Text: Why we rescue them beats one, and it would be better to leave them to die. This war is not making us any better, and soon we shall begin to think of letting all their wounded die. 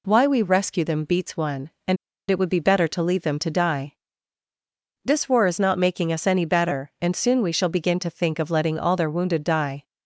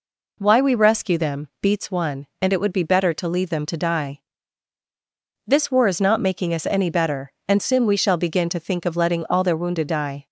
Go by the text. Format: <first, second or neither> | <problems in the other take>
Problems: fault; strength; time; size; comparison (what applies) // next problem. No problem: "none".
second | pauses between "and" and "it"; slight; at 1.9 s; 0.33 s long